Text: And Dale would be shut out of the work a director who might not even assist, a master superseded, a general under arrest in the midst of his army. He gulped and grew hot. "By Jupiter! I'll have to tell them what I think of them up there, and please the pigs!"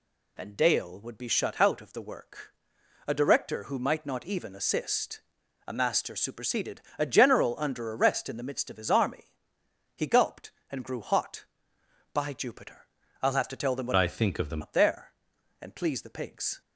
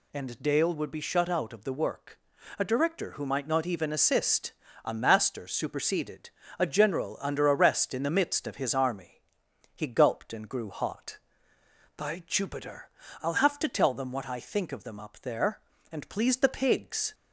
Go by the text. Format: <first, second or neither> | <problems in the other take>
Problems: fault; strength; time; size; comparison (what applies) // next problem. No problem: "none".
second | pauses between "work" and "a"; noticeable; at 2.5 s; 0.56 s long; also in the second // changes voice from "I" to "them"; from 13.9 to 14.6 s; 0.7 s long